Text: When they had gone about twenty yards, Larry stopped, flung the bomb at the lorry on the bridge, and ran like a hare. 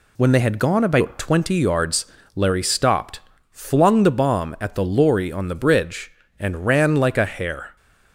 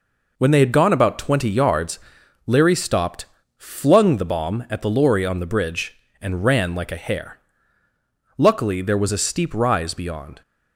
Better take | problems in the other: first | goes on to say "Luckily there was a steep rise beyond"; strong; from 8.3 s on; 2.0 s long

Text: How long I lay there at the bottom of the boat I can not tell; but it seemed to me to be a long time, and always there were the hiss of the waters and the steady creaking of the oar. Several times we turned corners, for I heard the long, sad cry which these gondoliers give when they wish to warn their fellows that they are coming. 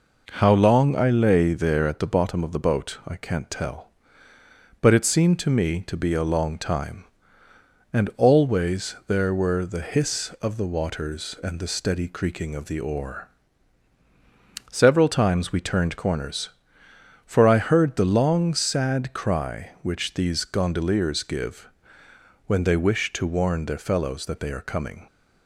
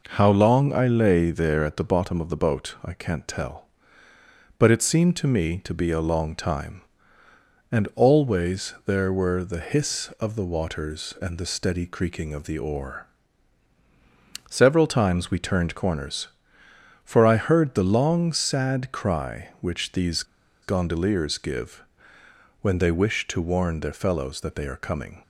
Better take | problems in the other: first | pauses between "these" and "gondoliers"; at 20.2 s; 0.38 s long // pauses between "give" and "when"; noticeable; at 21.8 s; 0.78 s long; noticeable in the first

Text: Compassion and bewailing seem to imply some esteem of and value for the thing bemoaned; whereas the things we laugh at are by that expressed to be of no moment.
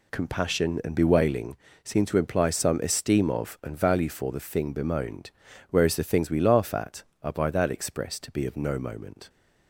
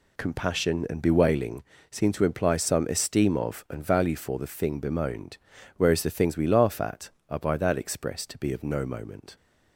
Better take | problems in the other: neither | pauses between "bewailing" and "seem"; slight; the same in both

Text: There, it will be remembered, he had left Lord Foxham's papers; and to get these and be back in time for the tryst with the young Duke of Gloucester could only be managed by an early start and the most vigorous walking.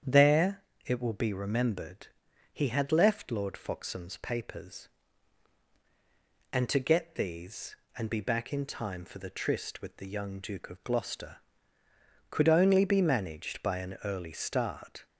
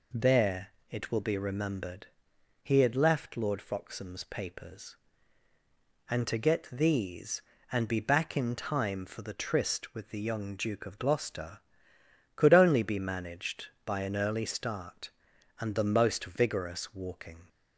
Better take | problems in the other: second | starts louder than the rest; strong; until 1.3 s; 8.5 dB // stops before "and the most vigorous walking"; at 15.0 s

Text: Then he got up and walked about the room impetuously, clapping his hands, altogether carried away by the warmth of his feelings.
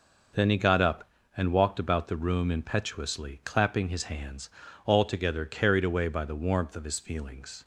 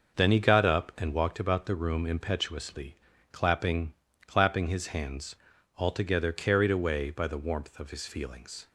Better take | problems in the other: first | starts louder than the rest; until 1.2 s; 6 dB // says "clapping" twice; at 4.2 s

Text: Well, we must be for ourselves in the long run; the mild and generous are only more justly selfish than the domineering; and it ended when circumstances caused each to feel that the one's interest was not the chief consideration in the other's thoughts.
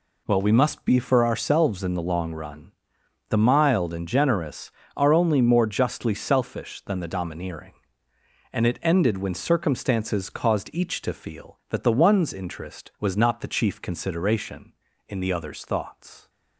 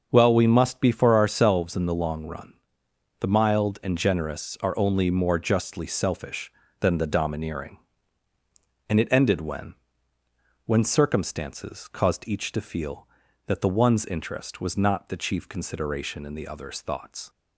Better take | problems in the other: first | starts louder than the rest; until 1.1 s; 6 dB // says "when" twice; at 10.6 s

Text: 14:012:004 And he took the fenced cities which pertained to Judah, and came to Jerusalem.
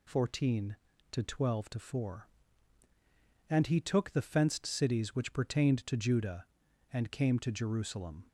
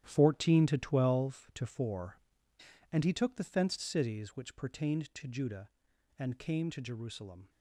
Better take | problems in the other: first | gets quieter; strong; throughout; 11 dB

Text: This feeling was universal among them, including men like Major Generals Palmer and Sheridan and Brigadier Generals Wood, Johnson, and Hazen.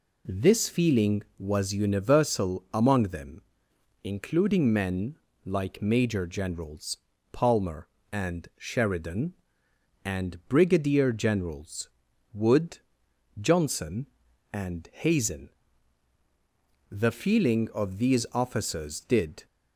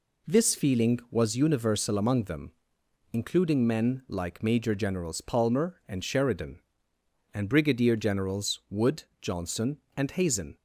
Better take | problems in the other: second | pauses between "men" and "like"; slight; at 5.1 s; 0.26 s long // pauses between "Generals" and "Palmer"; slight; at 6.9 s; 0.34 s long // pauses between "Generals" and "Wood"; noticeable; at 11.8 s; 0.46 s long // goes on to say "The feeling of these officers did"; strong; from 16.9 s on; 2.5 s long

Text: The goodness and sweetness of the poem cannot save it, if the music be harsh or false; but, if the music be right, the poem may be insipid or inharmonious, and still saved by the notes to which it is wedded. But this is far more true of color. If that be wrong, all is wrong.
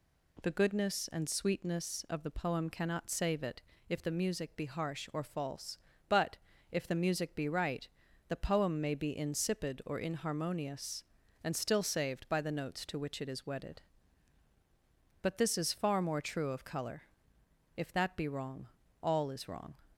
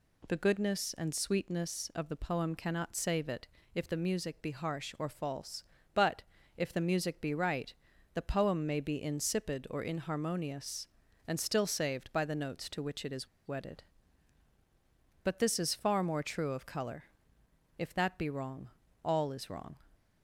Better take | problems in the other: first | pauses between "is" and "wedded"; slight; at 13.2 s; 0.19 s long

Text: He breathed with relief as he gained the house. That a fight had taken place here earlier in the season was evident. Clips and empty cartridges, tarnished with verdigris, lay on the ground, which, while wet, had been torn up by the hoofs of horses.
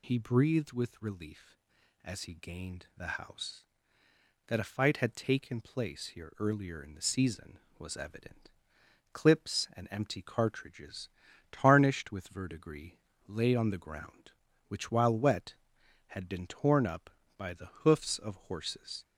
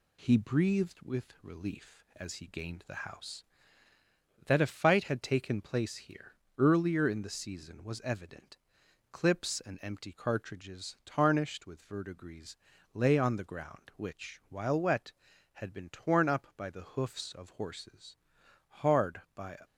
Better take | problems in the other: first | pauses between "here" and "earlier"; slight; at 6.3 s; 0.22 s long // goes on to say "Hard by"; noticeable; from 18.6 s on; 0.90 s long

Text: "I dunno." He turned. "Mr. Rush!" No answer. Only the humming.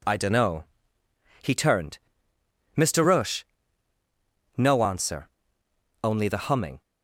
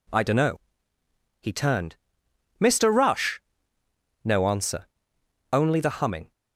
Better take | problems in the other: neither | none

